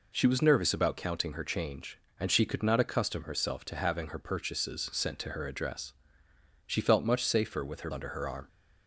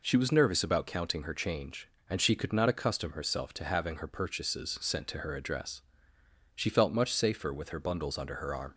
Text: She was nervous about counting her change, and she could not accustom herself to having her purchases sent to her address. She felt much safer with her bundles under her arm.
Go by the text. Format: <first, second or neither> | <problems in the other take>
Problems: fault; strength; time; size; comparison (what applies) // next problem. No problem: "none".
second | skips "bundles"; at 7.9 s